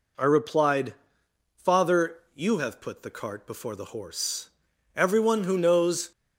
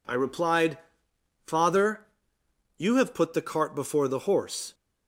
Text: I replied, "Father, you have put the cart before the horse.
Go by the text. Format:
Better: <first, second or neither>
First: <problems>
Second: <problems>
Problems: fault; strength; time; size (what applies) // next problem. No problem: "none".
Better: second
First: goes on to say "Everyone who knows"; noticeable; from 4.9 s on; 1.1 s long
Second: none